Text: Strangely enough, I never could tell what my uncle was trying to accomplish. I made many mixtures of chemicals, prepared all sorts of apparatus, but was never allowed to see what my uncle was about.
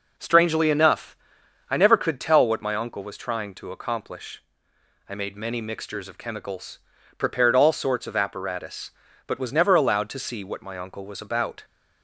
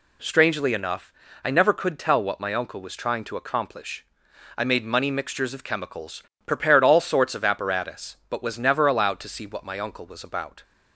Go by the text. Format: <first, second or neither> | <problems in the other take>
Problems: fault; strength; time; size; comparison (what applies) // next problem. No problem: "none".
first | says "money" for "many"; at 4.8 s